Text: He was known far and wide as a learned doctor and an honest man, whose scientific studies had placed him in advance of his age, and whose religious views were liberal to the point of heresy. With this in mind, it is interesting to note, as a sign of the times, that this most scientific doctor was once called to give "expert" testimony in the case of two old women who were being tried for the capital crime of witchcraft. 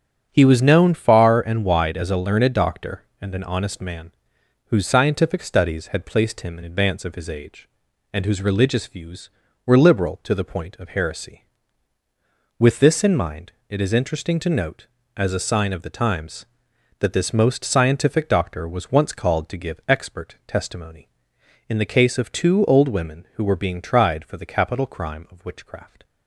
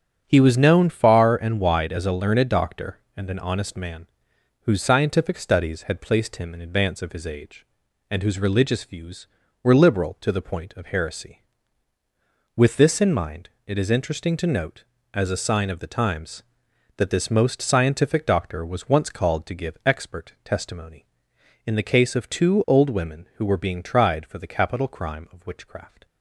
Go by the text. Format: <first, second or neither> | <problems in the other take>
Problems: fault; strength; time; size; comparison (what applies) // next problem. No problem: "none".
neither | starts louder than the rest; strong; the same in both